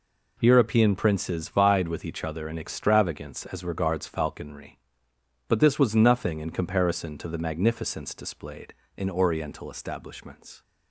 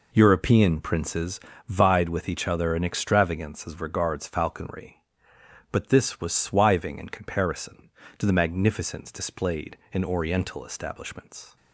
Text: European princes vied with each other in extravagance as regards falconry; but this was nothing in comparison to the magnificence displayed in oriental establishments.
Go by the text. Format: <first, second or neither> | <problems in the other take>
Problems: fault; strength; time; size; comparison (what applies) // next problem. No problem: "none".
first | pauses between "princes" and "vied"; slight; at 1.3 s; 0.30 s long // says "swiving" for "nothing"; at 6.3 s